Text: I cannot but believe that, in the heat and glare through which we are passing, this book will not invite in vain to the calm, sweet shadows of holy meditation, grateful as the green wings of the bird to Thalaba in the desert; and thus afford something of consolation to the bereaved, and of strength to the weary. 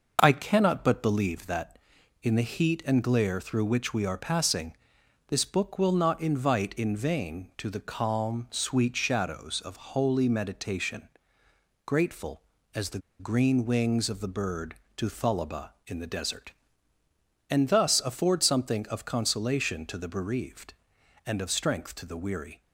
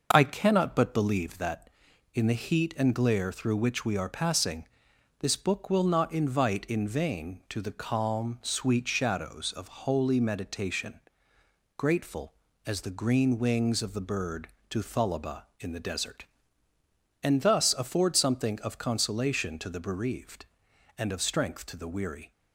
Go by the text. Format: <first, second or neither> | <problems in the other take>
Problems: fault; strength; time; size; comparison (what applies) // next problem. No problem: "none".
second | pauses between "the" and "green"; slight; at 12.9 s; 0.21 s long